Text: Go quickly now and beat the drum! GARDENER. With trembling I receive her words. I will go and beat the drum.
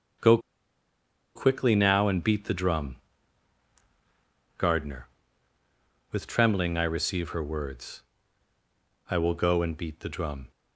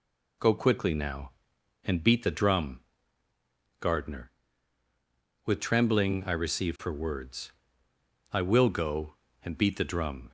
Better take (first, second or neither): second